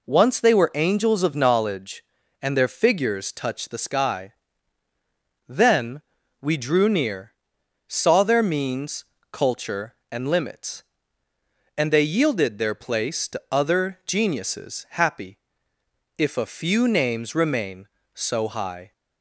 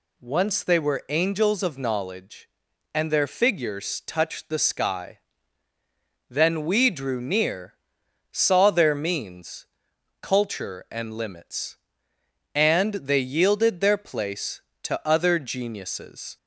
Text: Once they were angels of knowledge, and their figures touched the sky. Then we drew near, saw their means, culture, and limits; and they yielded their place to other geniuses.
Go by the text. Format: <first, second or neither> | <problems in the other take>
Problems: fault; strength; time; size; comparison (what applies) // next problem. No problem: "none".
second | pauses between "Then" and "we"; at 5.9 s; 0.40 s long // goes on to say "Happy if a few names remain so high"; strong; from 14.9 s on; 4.0 s long